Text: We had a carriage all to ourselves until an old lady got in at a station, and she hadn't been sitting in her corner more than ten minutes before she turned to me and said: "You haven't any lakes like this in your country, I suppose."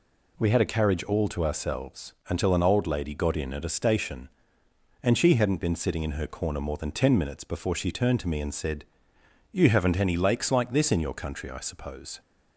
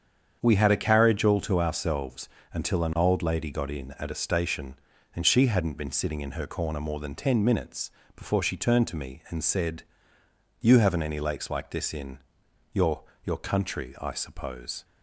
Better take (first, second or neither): first